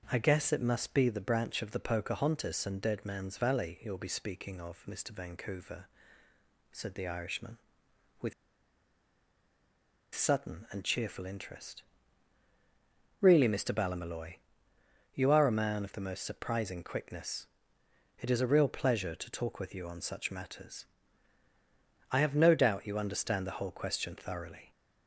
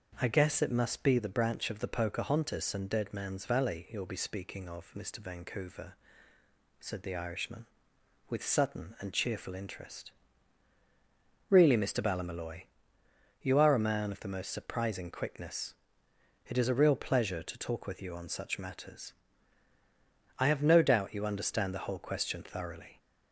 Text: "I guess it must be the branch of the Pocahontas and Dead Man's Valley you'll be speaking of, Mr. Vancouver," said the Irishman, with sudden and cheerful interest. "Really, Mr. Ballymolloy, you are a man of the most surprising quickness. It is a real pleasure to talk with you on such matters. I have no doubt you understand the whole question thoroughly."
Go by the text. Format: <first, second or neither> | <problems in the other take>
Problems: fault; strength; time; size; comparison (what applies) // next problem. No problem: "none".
second | starts louder than the rest; until 1.1 s; 6 dB; also in the second // pauses between "with" and "sudden"; strong; at 8.3 s; 1.8 s long